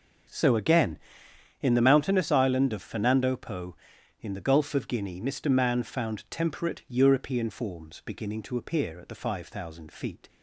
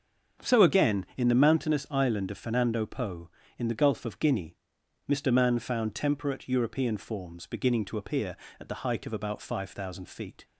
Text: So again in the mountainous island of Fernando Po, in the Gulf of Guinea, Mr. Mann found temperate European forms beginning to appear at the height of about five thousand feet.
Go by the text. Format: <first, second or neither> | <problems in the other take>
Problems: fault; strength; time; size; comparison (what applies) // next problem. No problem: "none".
second | starts louder than the rest; until 1.9 s; 6 dB; also in the second // skips "height of about"; at 9.1 s